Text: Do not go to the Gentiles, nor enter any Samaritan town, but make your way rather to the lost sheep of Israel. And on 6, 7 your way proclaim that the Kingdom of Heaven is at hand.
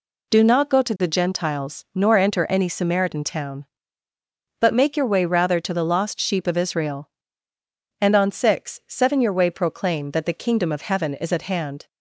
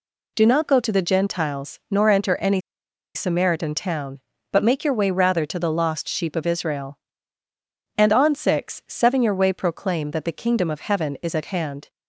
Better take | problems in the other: first | pauses between "any" and "Samaritan"; noticeable; at 2.5 s; 0.55 s long

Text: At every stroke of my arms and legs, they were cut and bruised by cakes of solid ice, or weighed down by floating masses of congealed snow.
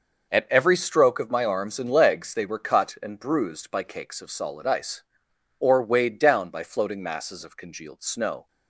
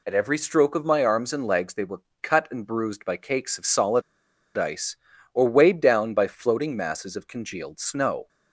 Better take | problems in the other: first | pauses between "were" and "cut"; slight; at 2.0 s; 0.22 s long // pauses between "solid" and "ice"; noticeable; at 4.0 s; 0.56 s long

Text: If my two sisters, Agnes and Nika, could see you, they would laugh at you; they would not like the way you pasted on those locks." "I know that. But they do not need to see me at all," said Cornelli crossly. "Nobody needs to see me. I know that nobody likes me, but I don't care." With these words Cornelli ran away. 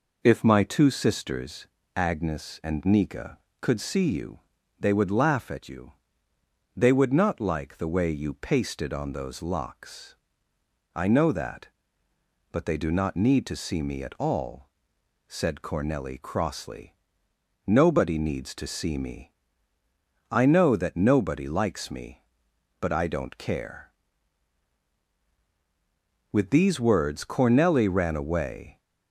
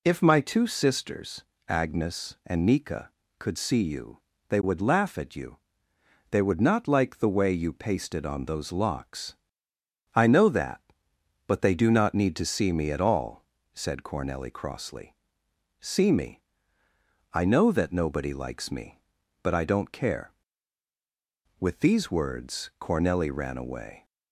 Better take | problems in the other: first | skips "Nobody needs to"; at 15.4 s

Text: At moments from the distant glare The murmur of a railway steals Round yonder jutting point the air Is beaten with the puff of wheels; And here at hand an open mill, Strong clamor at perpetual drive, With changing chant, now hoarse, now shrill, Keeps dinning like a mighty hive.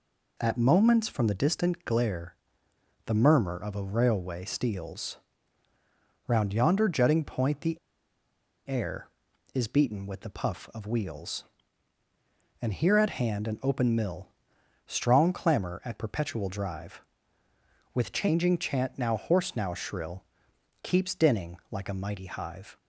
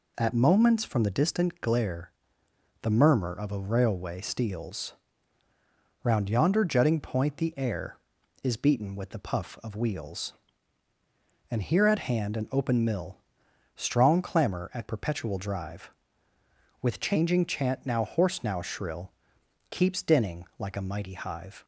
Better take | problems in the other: second | pauses between "glare" and "The"; noticeable; at 2.3 s; 0.70 s long; noticeable in the second // pauses between "steals" and "Round"; at 5.1 s; 1.1 s long; also in the second // pauses between "the" and "air"; noticeable; at 7.7 s; 0.93 s long

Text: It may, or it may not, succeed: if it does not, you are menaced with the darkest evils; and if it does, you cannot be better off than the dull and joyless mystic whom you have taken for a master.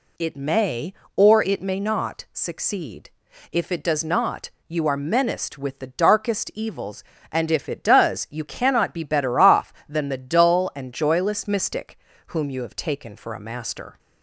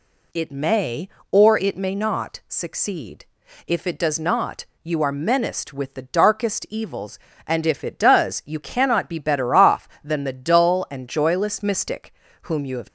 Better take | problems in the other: first | pauses between "mystic" and "whom"; slight; at 12.1 s; 0.30 s long; slight in the first // stops before "taken for a master"; at 12.8 s

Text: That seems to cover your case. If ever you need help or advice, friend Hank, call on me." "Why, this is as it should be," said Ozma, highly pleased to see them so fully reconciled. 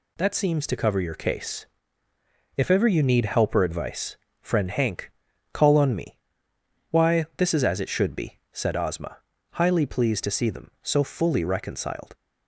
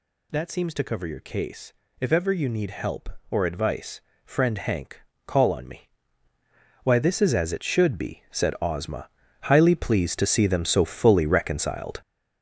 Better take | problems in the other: first | gets louder; strong; throughout; 7.5 dB

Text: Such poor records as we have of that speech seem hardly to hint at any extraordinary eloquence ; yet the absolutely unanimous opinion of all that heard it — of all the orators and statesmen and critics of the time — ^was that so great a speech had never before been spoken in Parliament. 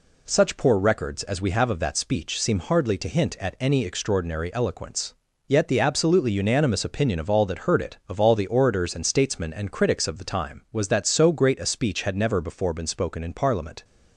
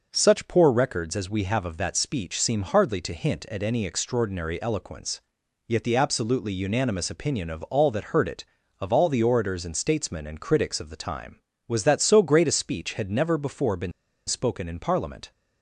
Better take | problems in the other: first | pauses between "been" and "spoken"; slight; at 13.9 s; 0.35 s long

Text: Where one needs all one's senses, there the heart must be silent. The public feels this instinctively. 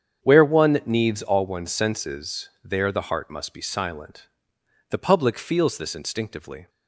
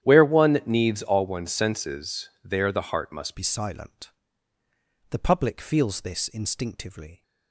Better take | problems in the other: first | starts louder than the rest; strong; until 1.0 s; 10.5 dB; strong in the first // changes voice at "be"; from 3.3 s on; 3.9 s long

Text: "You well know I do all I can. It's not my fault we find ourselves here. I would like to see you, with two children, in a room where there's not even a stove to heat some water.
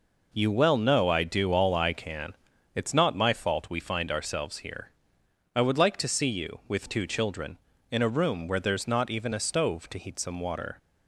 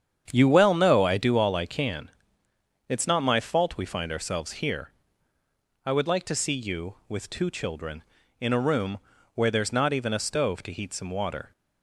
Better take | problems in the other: first | starts louder than the rest; strong; until 1.3 s; 8 dB // pauses between "room" and "where"; at 8.9 s; 0.38 s long

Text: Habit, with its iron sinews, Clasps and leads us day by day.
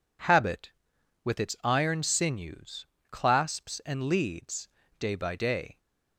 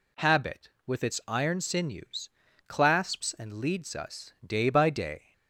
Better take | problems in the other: second | skips "us"; at 4.8 s

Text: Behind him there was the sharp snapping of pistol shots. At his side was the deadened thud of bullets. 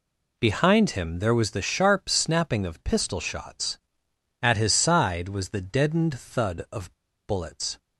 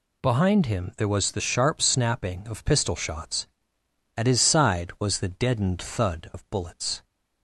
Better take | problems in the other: second | pauses between "of" and "bullets"; slight; at 6.9 s; 0.30 s long

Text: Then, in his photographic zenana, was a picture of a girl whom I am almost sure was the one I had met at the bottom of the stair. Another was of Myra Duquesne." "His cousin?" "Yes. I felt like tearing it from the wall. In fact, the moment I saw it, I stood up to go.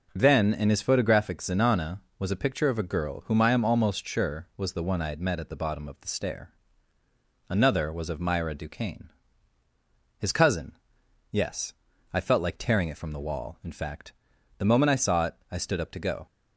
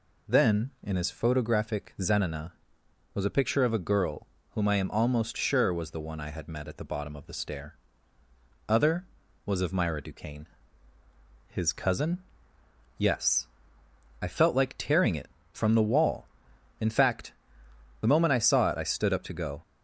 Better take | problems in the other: first | pauses between "girl" and "whom"; slight; at 4.2 s; 0.26 s long // says "Other" for "Another"; at 8.6 s

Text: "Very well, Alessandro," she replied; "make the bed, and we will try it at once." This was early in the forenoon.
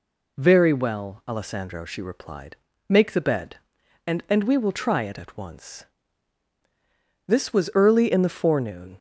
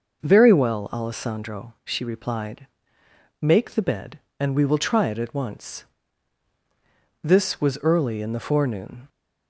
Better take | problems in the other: second | says "and" twice; at 4.2 s

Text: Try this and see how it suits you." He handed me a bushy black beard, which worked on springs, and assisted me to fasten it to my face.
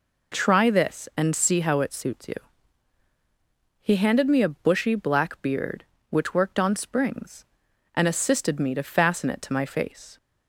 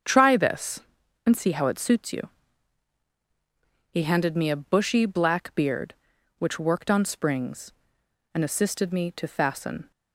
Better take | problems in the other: first | starts louder than the rest; strong; until 1.4 s; 7 dB // stops before "it to my face"; at 9.9 s

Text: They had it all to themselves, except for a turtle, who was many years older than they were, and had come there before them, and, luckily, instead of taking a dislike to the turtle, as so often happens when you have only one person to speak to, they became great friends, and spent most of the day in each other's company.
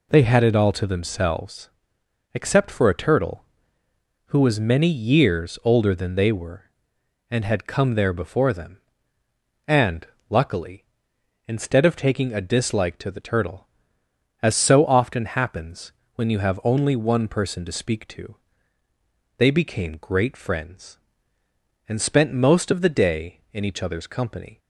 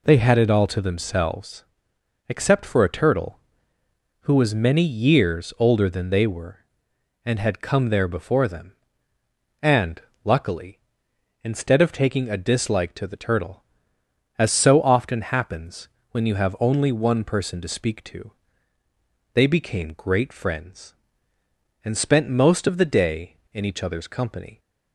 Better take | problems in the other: neither | pauses between "happens" and "when"; slight; the same in both

